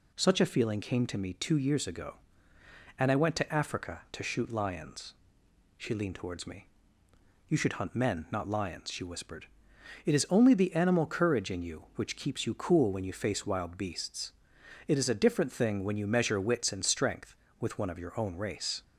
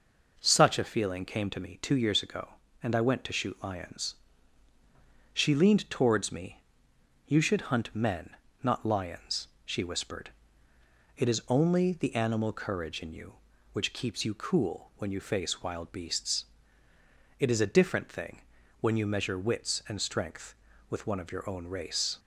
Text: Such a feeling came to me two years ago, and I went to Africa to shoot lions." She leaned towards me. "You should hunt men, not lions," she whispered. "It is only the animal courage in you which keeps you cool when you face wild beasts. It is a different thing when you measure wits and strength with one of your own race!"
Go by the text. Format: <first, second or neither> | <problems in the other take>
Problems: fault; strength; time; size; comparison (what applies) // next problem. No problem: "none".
first | skips "Africa to"; at 3.3 s // pauses between "thing" and "when"; at 18.4 s; 0.38 s long